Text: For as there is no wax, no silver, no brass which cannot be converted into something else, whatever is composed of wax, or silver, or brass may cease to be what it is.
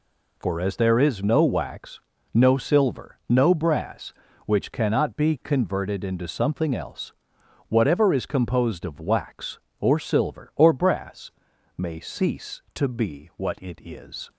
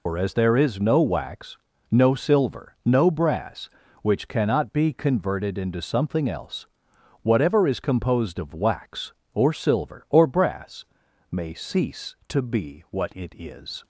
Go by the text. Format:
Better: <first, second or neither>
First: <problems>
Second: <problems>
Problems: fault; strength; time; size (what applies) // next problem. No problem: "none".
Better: first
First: pauses between "brass" and "may"; noticeable; at 11.3 s; 0.46 s long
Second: loses the start of "For"; at 0.0 s; 105 ms // pauses between "brass" and "may"; noticeable; at 10.8 s; 0.46 s long